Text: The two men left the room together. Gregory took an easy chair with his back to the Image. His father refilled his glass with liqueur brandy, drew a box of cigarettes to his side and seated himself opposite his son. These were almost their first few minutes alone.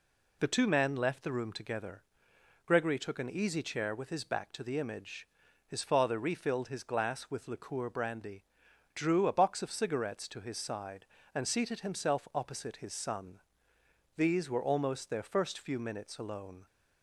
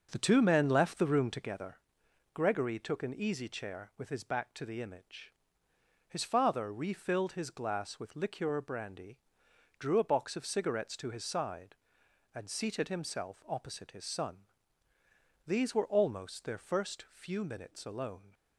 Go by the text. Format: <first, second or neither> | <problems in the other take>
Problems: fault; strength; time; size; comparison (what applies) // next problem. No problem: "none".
first | starts louder than the rest; until 1.8 s; 6.5 dB